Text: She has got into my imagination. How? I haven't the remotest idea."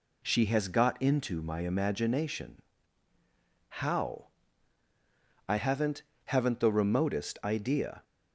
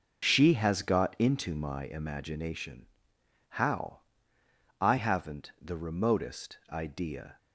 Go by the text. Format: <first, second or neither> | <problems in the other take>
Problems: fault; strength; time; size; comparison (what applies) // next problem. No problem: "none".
second | says "haven't" twice; at 6.2 s